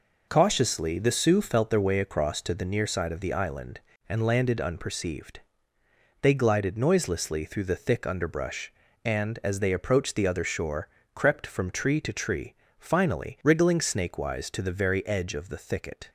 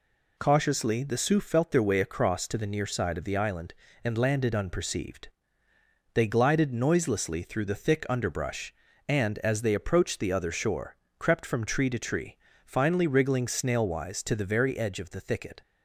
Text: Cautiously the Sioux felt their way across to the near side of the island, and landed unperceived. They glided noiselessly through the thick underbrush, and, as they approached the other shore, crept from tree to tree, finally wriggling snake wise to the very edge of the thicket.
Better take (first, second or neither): first